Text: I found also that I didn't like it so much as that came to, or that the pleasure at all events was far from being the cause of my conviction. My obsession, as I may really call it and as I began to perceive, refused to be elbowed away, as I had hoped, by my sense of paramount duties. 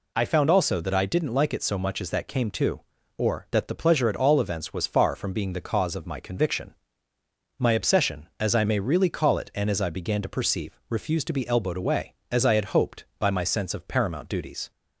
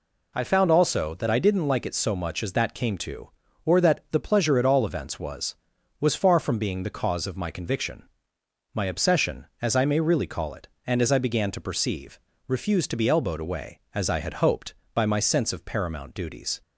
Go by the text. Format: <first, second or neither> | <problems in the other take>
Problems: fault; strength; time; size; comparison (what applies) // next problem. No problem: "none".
first | says "was" twice; at 5.9 s